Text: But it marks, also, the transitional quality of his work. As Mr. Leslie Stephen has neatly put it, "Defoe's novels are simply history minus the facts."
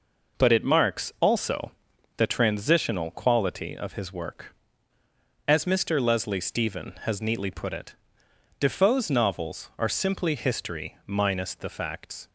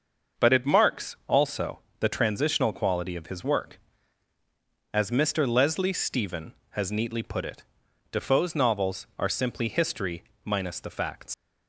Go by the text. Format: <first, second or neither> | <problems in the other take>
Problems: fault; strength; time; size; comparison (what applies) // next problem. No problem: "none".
first | starts louder than the rest; until 1.5 s; 6.5 dB // pauses between "history" and "minus"; slight; at 10.2 s; 0.20 s long // leaves "facts" unfinished; at 11.3 s; 80 ms